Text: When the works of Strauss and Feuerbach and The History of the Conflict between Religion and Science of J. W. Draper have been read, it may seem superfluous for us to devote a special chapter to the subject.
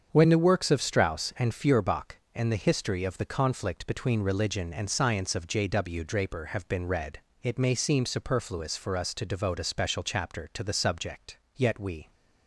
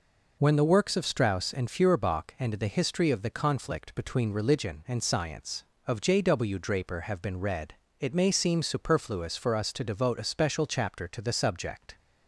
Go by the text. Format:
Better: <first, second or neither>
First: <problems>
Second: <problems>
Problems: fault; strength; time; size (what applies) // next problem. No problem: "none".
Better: second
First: starts louder than the rest; strong; until 1.1 s; 7 dB // goes on to say "Yet we"; from 11.5 s on; 0.56 s long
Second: none